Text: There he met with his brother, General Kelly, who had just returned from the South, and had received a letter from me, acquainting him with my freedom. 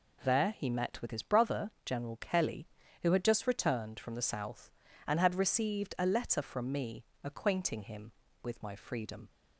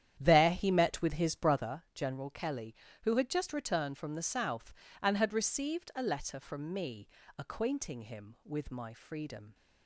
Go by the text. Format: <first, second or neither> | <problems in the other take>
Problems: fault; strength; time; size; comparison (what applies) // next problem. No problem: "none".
first | starts louder than the rest; strong; until 1.7 s; 10 dB